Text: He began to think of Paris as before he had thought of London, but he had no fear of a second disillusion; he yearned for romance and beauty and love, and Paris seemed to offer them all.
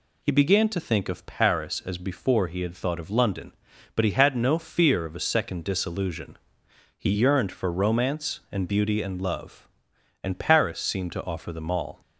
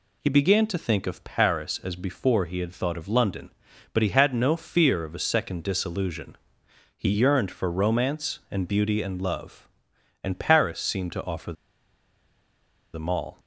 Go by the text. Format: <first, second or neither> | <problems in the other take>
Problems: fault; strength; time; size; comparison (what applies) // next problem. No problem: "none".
first | pauses between "offer" and "them"; strong; at 11.5 s; 1.4 s long